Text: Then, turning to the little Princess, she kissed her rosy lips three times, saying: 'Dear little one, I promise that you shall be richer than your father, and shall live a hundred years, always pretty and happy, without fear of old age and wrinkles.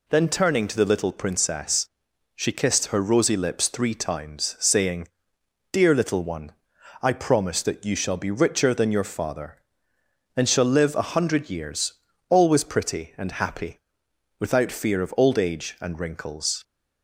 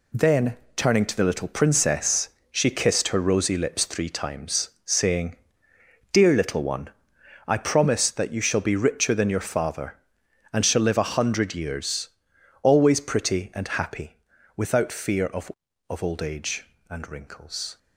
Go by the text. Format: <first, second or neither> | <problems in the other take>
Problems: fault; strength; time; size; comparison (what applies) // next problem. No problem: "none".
first | says "of" twice; at 15.8 s